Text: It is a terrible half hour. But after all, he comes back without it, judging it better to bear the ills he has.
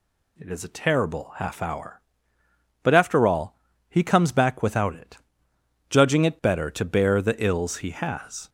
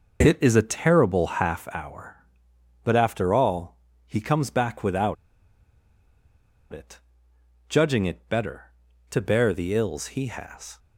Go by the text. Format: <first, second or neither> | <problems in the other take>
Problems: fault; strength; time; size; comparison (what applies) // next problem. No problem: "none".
first | pauses between "without" and "it"; strong; at 5.1 s; 1.5 s long